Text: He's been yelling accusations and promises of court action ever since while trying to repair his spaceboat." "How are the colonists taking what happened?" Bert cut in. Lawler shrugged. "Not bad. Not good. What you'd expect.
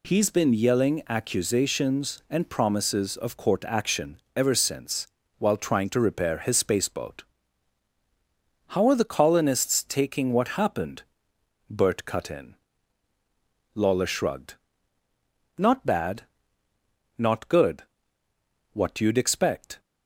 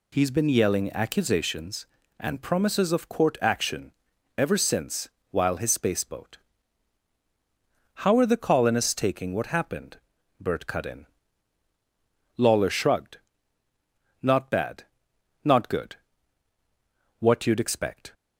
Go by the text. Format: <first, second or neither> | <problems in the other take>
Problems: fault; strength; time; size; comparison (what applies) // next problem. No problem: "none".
first | pauses between "action" and "ever"; at 3.9 s; 0.44 s long; slight in the first // pauses between "since" and "while"; slight; at 5.0 s; 0.22 s long; slight in the first // skips "trying to repair"; at 5.5 s